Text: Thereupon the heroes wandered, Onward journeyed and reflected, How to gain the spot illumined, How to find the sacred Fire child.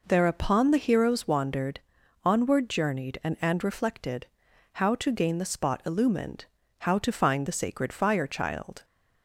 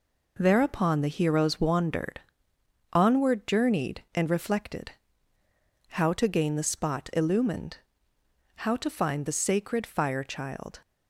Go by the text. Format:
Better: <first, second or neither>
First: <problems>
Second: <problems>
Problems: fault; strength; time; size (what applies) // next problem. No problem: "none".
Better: second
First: says "and" twice; at 3.4 s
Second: none